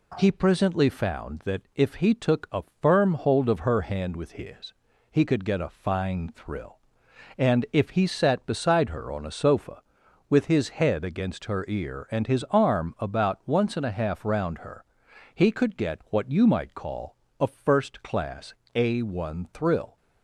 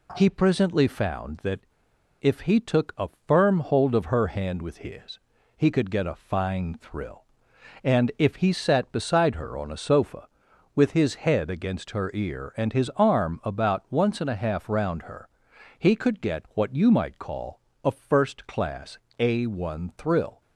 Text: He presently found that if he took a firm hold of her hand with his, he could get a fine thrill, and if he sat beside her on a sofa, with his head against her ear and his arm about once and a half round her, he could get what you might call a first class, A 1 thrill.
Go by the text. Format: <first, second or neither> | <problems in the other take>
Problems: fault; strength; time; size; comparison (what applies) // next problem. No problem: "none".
first | pauses between "that" and "if"; noticeable; at 1.6 s; 0.59 s long // pauses between "a" and "firm"; slight; at 3.0 s; 0.18 s long; slight in the first // pauses between "call" and "a"; slight; at 17.6 s; 0.24 s long; slight in the first